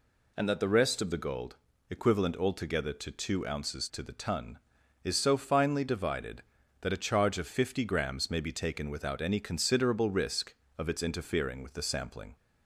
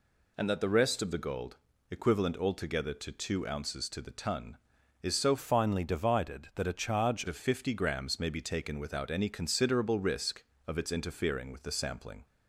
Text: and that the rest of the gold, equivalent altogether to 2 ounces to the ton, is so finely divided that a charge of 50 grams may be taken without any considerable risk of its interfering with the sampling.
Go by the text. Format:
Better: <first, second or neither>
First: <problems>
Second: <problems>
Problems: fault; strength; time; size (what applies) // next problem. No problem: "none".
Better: first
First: none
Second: changes voice from "finely" to "charge"; from 5.3 to 7.2 s; 1.9 s long